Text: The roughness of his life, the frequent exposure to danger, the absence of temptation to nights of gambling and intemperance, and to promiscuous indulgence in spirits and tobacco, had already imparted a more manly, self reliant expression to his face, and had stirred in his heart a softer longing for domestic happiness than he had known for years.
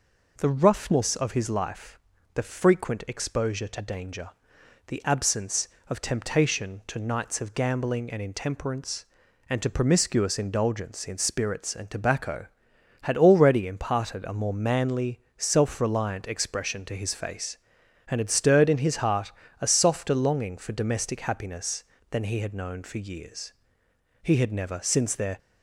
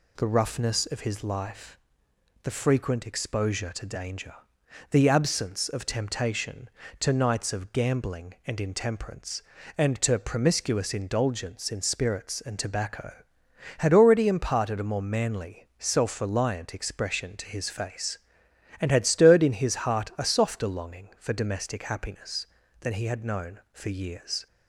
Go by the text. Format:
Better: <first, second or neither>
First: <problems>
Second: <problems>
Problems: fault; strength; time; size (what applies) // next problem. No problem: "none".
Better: second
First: pauses between "heart" and "a"; slight; at 19.3 s; 0.30 s long // goes on to say "He had never since their"; noticeable; from 24.2 s on; 1.1 s long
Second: none